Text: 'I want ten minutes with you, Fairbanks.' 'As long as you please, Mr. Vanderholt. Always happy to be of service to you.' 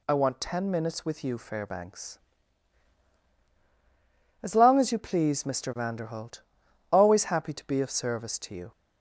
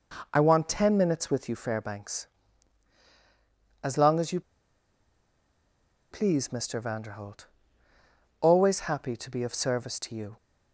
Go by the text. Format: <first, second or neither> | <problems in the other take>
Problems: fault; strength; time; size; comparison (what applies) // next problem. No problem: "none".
first | pauses between "you" and "please"; strong; at 4.4 s; 1.7 s long